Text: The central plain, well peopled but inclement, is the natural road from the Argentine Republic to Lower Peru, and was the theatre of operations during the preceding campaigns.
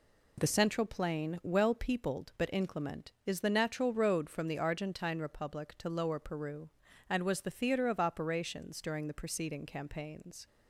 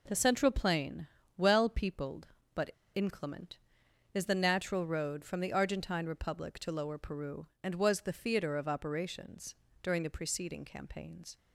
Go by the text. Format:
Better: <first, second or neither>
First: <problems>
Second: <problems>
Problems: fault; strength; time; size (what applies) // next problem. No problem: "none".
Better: first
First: none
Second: pauses between "but" and "inclement"; slight; at 2.7 s; 0.24 s long // pauses between "operations" and "during"; slight; at 9.5 s; 0.30 s long